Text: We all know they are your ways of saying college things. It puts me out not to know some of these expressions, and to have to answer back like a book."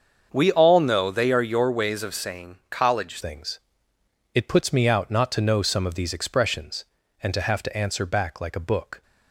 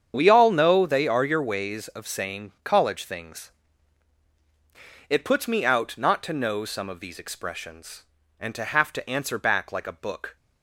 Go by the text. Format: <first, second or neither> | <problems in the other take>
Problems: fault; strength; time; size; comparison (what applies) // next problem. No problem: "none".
second | starts louder than the rest; until 1.3 s; 7 dB; strong in the second // changes voice at "things"; from 3.2 s on; 5.8 s long